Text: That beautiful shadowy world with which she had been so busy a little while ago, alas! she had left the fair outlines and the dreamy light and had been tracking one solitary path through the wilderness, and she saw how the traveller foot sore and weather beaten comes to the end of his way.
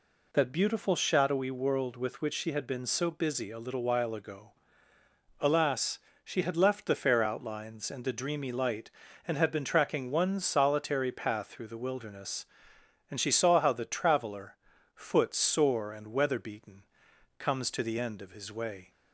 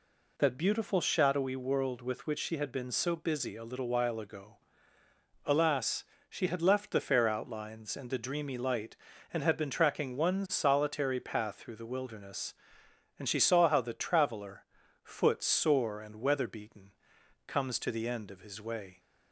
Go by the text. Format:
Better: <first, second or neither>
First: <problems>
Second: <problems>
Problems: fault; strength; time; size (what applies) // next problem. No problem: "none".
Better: neither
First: pauses between "traveller" and "foot"; at 14.5 s; 0.40 s long // pauses between "beaten" and "comes"; noticeable; at 16.8 s; 0.56 s long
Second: pauses between "traveller" and "foot"; at 14.6 s; 0.40 s long // pauses between "beaten" and "comes"; noticeable; at 16.9 s; 0.56 s long